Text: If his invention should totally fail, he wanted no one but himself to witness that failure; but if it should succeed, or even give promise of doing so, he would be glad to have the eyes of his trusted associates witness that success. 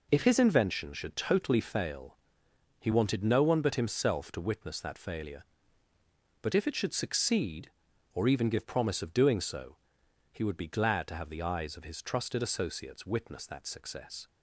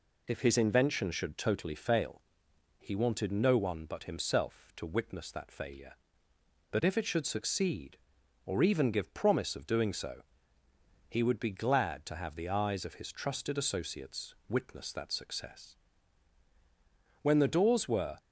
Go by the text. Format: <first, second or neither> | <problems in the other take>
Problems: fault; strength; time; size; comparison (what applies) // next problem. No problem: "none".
first | pauses between "associates" and "witness"; slight; at 14.3 s; 0.16 s long // goes on to say "When the doors were"; noticeable; from 17.2 s on; 0.94 s long